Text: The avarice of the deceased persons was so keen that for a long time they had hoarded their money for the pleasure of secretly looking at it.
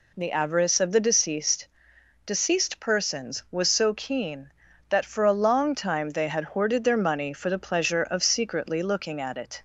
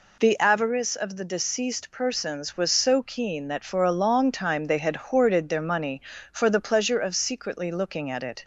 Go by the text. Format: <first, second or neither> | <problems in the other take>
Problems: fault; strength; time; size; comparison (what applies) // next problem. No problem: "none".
second | says "deceased" twice; at 2.2 s